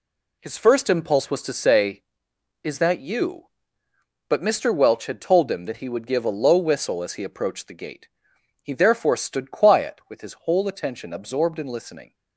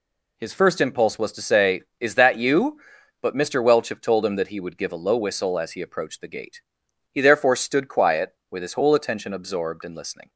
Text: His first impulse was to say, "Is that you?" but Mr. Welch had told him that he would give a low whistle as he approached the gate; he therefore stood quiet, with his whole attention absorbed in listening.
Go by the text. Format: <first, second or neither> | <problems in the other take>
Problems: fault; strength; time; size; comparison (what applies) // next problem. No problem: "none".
first | says "have" for "had"; at 3.8 s